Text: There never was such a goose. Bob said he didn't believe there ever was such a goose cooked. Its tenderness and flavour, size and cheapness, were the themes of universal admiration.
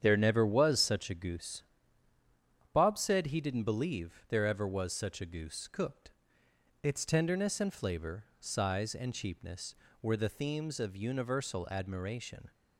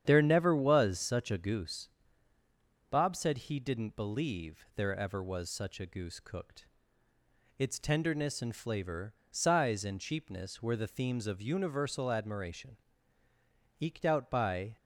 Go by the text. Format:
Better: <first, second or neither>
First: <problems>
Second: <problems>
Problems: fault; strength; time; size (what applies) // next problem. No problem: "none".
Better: first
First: starts louder than the rest; strong; until 1.0 s; 8.5 dB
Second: starts louder than the rest; strong; until 1.0 s; 9 dB // goes on to say "Eked out by"; noticeable; from 13.8 s on; 0.96 s long